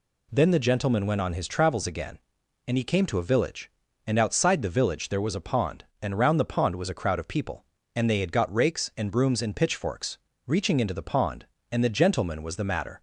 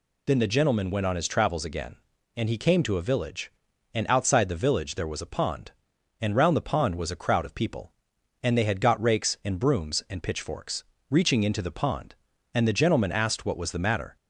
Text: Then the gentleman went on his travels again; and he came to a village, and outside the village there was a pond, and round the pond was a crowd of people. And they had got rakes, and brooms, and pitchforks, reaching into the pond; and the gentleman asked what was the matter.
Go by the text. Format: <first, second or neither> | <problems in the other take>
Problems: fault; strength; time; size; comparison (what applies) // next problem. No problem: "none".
second | skips "asked what"; at 12.4 s